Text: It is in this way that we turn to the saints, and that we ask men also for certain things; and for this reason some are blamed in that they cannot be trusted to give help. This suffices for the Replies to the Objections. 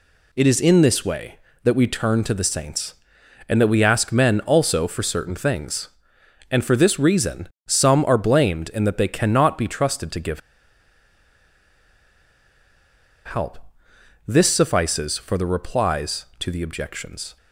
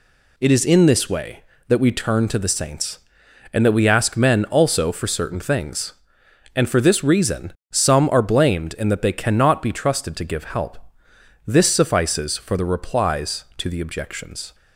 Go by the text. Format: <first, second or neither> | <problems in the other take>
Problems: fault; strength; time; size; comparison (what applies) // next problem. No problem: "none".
second | pauses between "reason" and "some"; slight; at 7.4 s; 0.18 s long; slight in the second // pauses between "give" and "help"; strong; at 10.3 s; 2.8 s long